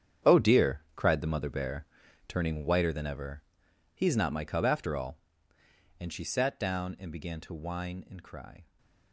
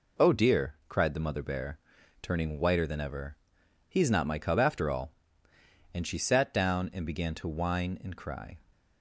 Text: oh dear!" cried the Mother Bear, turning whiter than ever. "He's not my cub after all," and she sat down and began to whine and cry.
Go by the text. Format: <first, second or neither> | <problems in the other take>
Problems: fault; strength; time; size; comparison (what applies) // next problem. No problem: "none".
second | gets quieter; strong; throughout; 12.5 dB